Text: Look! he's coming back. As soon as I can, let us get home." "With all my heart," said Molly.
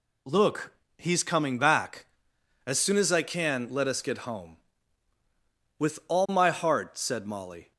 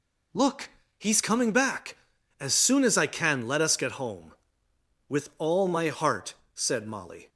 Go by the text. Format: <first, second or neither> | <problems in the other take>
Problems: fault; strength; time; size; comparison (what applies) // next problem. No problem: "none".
neither | none